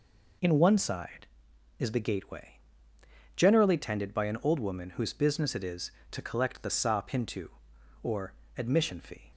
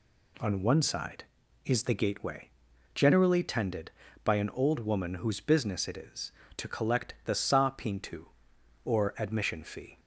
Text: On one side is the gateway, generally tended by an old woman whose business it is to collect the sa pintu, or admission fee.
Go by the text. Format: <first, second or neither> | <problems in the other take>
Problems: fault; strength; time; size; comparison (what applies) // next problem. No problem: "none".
second | says "In" for "On"; at 0.4 s // pauses between "or" and "admission"; slight; at 8.3 s; 0.24 s long